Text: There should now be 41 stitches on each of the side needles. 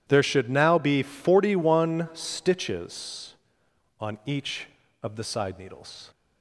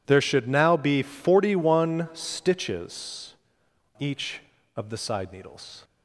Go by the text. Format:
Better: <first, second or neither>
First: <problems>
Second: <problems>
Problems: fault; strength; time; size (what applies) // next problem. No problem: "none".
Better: first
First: none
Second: skips "on"; at 3.6 s